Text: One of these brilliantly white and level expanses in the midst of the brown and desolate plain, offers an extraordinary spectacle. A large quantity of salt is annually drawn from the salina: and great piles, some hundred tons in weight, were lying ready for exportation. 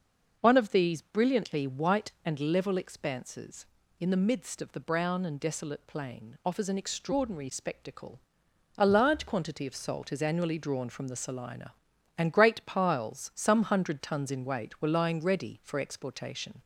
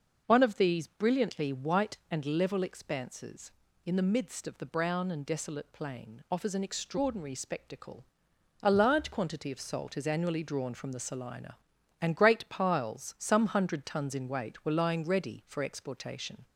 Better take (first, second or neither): neither